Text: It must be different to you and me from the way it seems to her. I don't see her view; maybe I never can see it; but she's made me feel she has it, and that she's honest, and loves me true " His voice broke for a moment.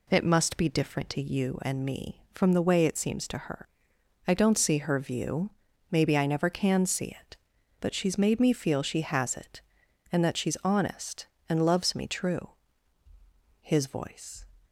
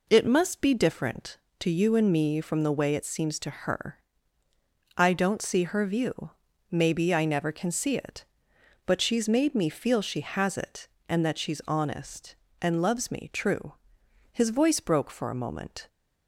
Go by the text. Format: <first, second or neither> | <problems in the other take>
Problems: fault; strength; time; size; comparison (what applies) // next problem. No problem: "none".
second | stops before "broke for a moment"; at 14.6 s